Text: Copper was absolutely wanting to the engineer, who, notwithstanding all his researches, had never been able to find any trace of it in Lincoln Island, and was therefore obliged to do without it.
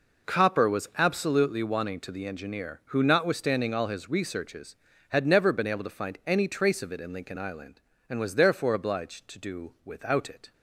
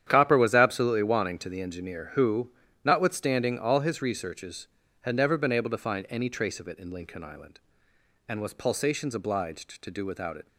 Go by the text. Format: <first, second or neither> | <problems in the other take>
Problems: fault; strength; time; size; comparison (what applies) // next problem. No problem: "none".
first | starts louder than the rest; strong; until 1.0 s; 9.5 dB // says "pulsations" for "therefore"; at 8.5 s